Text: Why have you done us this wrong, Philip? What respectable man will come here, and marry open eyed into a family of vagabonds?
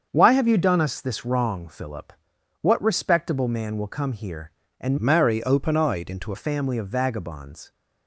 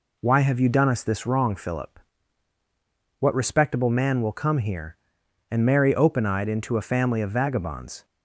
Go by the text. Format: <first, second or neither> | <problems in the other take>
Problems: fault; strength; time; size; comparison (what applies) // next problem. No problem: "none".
second | starts louder than the rest; until 1.1 s; 7 dB // changes voice from "marry" to "into"; from 4.9 to 6.3 s; 1.4 s long